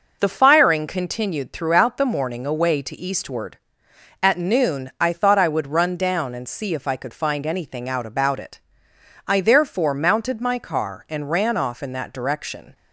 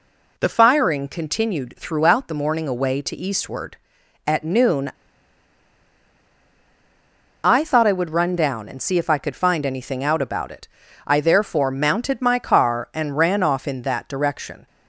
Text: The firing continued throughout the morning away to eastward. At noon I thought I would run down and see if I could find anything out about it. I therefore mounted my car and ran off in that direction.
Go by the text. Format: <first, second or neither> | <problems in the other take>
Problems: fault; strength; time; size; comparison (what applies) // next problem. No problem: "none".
first | pauses between "noon" and "I"; strong; at 4.9 s; 2.5 s long